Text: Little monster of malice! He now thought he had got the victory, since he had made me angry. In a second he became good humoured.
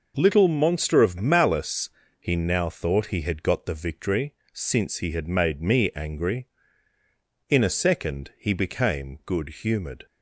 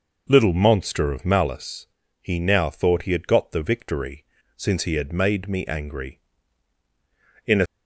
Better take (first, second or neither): first